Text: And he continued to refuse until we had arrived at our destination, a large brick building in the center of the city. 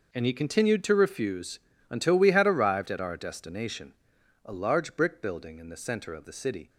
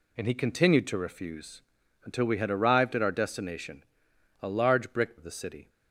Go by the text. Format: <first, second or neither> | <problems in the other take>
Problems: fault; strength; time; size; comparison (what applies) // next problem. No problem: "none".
first | pauses between "refuse" and "until"; at 1.6 s; 0.42 s long; slight in the first // skips "building in the center"; at 5.1 s